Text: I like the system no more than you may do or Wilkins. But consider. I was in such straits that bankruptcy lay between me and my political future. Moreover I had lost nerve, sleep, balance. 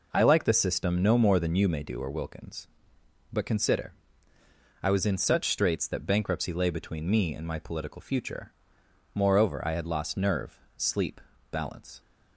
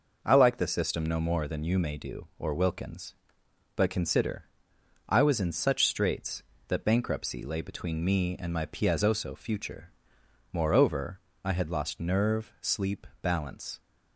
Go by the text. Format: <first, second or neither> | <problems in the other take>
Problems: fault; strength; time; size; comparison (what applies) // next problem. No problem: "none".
first | says "piazzoso" for "political"; at 8.6 s // pauses between "Moreover" and "I"; slight; at 11.1 s; 0.24 s long